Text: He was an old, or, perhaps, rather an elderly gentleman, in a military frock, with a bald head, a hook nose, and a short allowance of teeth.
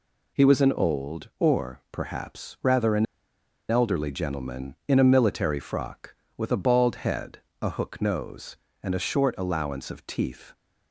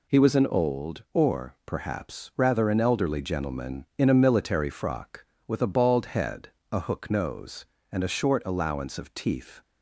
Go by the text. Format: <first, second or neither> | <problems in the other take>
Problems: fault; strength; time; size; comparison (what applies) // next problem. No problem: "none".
second | pauses between "an" and "elderly"; noticeable; at 3.0 s; 0.64 s long